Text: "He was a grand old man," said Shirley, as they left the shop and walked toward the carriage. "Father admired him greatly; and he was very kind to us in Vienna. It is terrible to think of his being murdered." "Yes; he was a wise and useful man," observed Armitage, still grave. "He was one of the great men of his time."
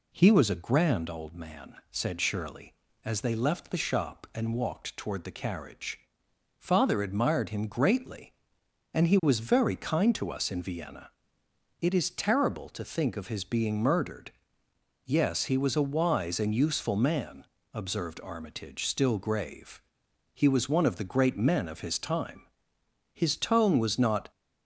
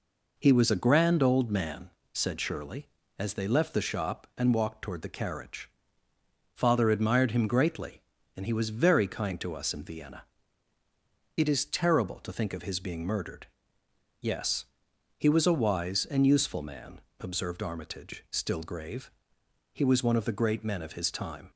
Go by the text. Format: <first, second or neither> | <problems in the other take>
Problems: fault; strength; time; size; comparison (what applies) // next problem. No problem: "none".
second | goes on to say "His tone was not"; noticeable; from 23.2 s on; 1.1 s long